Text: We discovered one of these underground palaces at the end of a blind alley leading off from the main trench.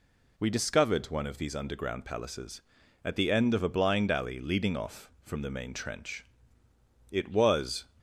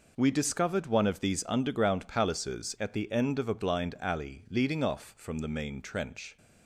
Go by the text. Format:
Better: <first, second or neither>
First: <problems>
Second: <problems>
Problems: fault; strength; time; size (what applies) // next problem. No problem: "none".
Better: second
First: goes on to say "It was"; noticeable; from 7.1 s on; 0.76 s long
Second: none